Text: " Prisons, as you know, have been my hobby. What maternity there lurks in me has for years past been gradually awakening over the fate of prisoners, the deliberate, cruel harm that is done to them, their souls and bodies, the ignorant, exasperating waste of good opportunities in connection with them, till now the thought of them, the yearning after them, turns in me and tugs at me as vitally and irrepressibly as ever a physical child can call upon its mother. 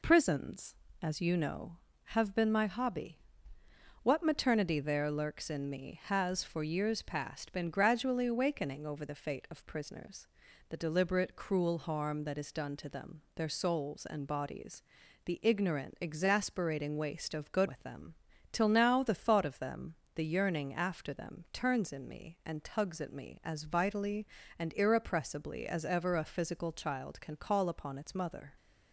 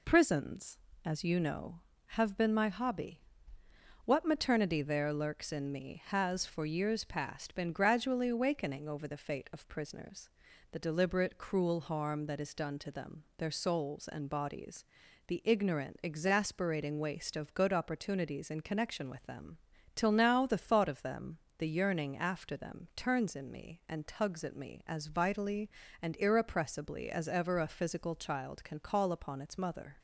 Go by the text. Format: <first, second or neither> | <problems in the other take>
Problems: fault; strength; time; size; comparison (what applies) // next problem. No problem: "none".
second | skips "opportunities in connection"; at 17.6 s